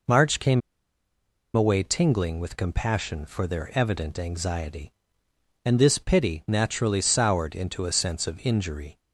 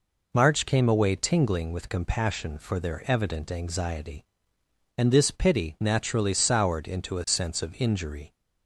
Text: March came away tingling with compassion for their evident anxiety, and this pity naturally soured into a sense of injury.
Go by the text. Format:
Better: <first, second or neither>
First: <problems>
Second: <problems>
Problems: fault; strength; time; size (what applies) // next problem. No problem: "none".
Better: second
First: pauses between "came" and "away"; noticeable; at 0.6 s; 0.94 s long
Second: none